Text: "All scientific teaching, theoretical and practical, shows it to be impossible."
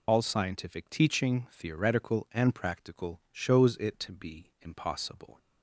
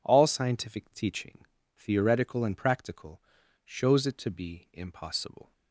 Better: second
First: loses the start of "All"; at 0.0 s; 85 ms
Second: none

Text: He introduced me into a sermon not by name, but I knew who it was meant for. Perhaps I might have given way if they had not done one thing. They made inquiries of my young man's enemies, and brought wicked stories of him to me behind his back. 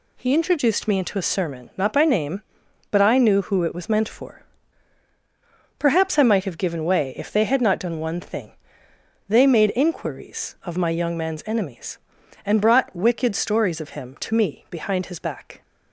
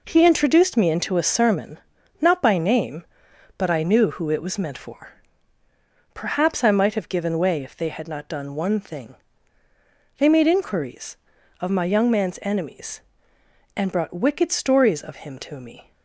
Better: first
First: none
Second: pauses between "sermon" and "not"; at 1.7 s; 0.42 s long // stops before "behind his back"; at 15.9 s

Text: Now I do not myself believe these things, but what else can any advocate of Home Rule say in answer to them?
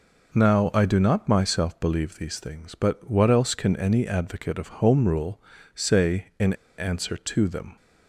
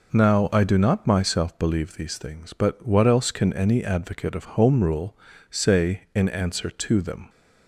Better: second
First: pauses between "Rule" and "say"; slight; at 5.4 s; 0.32 s long // pauses between "in" and "answer"; slight; at 6.5 s; 0.24 s long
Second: pauses between "Rule" and "say"; slight; at 5.1 s; 0.32 s long

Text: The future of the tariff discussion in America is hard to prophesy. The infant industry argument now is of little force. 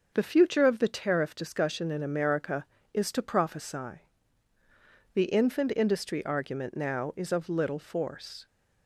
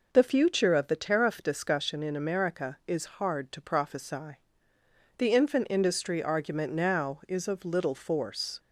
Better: second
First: starts louder than the rest; until 1.1 s; 6.5 dB // skips "hard"; at 3.1 s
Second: none

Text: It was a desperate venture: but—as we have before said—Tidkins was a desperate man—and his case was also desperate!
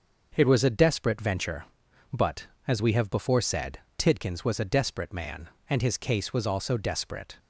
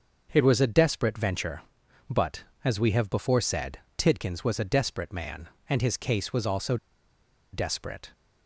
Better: first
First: starts louder than the rest; until 1.3 s; 6.5 dB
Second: starts louder than the rest; until 1.3 s; 6.5 dB // pauses between "also" and "desperate"; noticeable; at 6.7 s; 0.77 s long

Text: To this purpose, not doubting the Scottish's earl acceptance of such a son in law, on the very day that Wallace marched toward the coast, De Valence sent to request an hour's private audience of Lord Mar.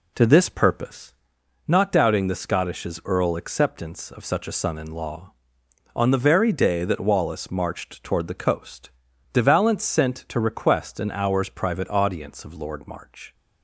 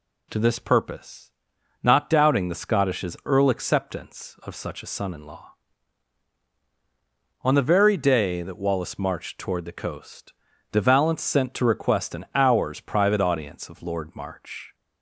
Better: second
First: starts louder than the rest; slight; until 1.4 s; 2.5 dB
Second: none

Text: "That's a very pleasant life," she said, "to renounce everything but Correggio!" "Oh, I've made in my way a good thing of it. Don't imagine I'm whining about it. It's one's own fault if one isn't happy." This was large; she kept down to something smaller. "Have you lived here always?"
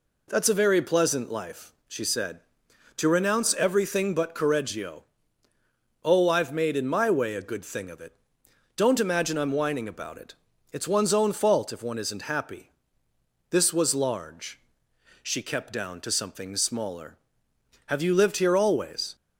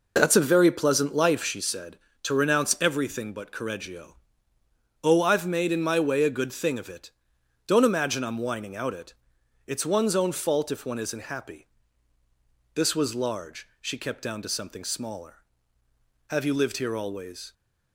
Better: first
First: none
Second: says "out" for "about"; at 8.7 s

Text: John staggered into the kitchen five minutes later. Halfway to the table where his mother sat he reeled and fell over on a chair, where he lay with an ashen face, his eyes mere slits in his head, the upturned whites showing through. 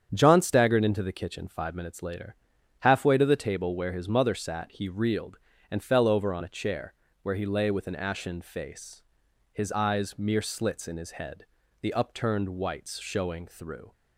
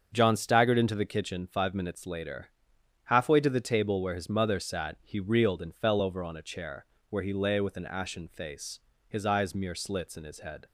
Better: first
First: starts louder than the rest; strong; until 1.1 s; 8.5 dB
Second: starts louder than the rest; until 1.1 s; 7 dB // stops before "the upturned whites showing through"; at 10.6 s

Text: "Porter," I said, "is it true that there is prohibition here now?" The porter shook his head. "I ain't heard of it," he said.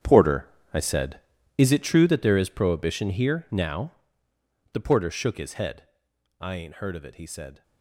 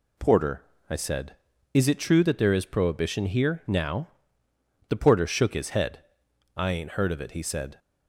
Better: second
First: gets quieter; strong; throughout; 14 dB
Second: none

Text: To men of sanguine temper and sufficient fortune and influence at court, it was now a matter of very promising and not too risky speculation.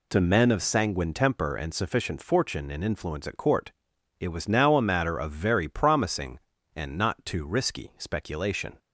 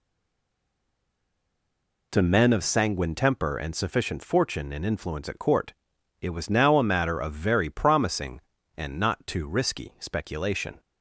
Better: first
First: none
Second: stays silent before the first word; until 2.1 s; 2.1 s long

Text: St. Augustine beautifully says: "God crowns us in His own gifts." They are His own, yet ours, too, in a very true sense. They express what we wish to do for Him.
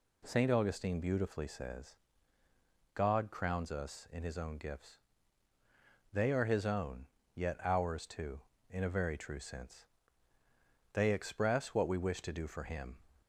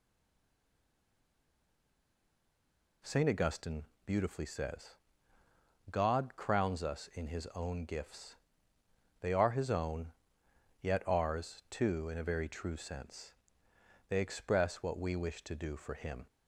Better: first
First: none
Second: stays silent before the first word; strong; until 3.0 s; 3.0 s long // pauses between "Augustine" and "beautifully"; slight; at 3.8 s; 0.22 s long

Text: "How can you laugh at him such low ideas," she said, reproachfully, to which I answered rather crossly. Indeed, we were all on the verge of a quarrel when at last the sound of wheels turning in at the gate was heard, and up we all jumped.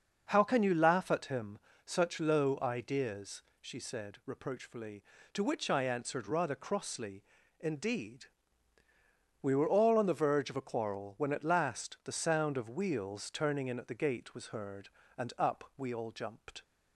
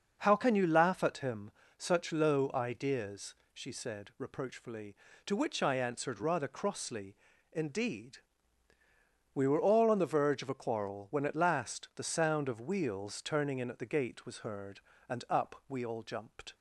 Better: neither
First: starts louder than the rest; noticeable; until 1.3 s; 6 dB // pauses between "him" and "such"; slight; at 1.5 s; 0.28 s long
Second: starts louder than the rest; noticeable; until 1.2 s; 6 dB // pauses between "him" and "such"; slight; at 1.5 s; 0.28 s long

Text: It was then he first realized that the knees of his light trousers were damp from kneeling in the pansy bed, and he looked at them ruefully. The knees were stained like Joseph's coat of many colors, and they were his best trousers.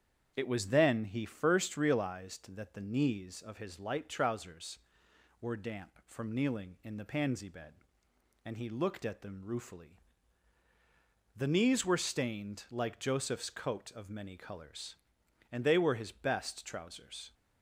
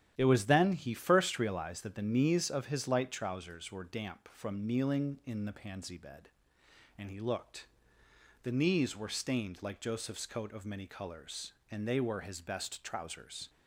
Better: first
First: starts louder than the rest; strong; until 1.3 s; 8 dB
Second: starts louder than the rest; strong; until 1.1 s; 11 dB // skips "at them ruefully"; at 8.0 s

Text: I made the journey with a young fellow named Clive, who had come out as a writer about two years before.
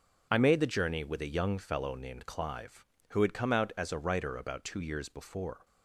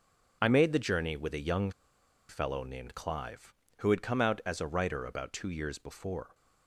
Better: first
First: none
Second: pauses between "young" and "fellow"; noticeable; at 1.7 s; 0.58 s long

